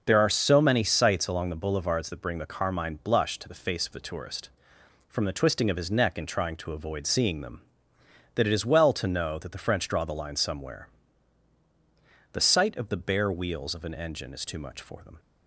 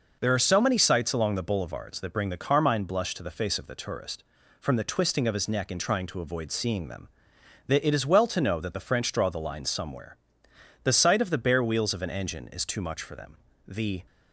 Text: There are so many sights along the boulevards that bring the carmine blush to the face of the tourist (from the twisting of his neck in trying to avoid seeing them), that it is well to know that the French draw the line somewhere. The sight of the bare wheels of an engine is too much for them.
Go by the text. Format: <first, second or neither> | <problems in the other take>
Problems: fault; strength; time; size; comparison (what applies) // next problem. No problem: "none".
first | goes on to say "The"; slight; from 13.6 s on; 0.38 s long